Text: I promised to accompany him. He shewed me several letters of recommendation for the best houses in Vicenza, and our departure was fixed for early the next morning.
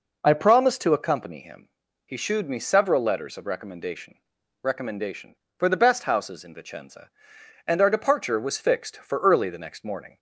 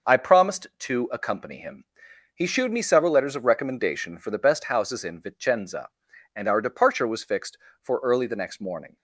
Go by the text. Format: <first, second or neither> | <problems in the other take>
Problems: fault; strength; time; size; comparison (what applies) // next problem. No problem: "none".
second | says "recommendation" twice; at 4.6 s